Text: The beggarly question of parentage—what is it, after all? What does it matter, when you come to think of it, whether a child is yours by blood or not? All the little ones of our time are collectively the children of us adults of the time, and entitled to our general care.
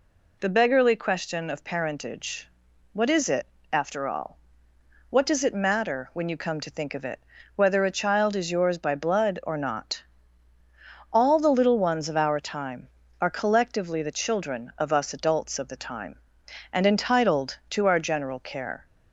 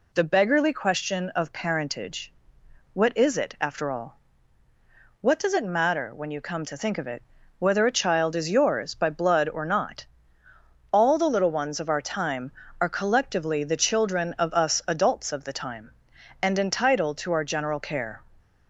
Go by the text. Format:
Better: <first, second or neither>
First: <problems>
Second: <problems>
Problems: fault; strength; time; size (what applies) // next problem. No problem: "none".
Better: neither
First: none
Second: none